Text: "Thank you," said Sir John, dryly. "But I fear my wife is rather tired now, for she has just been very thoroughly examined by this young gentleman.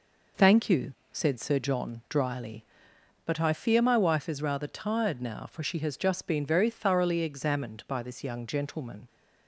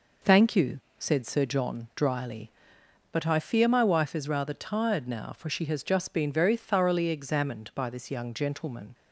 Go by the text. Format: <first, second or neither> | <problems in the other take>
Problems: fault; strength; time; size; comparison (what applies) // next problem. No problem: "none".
neither | none